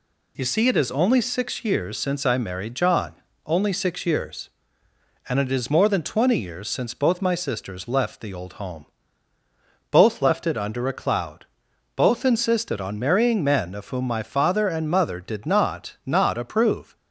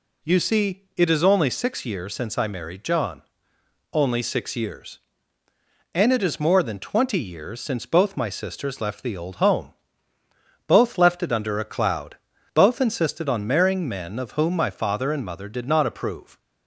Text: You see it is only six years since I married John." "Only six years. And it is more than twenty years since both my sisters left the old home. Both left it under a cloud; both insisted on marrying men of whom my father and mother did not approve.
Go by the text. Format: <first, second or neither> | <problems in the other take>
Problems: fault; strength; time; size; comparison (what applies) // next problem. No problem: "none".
second | says "not" twice; at 16.0 s